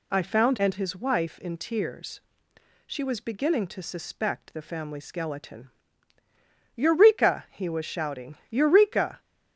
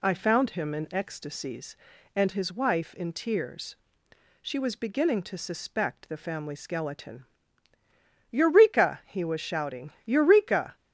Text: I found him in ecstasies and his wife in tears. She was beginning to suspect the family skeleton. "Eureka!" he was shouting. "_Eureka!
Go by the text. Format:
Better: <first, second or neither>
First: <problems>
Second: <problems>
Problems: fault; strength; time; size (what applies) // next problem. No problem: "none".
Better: second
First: skips "him in ecstasies"; at 0.5 s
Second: none